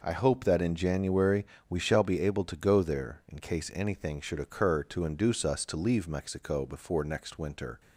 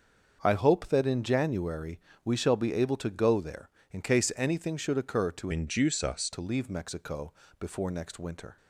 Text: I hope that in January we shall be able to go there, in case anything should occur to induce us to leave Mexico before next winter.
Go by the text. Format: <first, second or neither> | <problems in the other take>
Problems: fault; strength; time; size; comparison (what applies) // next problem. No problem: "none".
first | starts louder than the rest; until 1.4 s; 6.5 dB // pauses between "January" and "we"; slight; at 1.9 s; 0.26 s long; slight in the first // changes voice from "induce" to "us"; from 5.5 to 6.2 s; 0.7 s long // pauses between "Mexico" and "before"; slight; at 7.3 s; 0.26 s long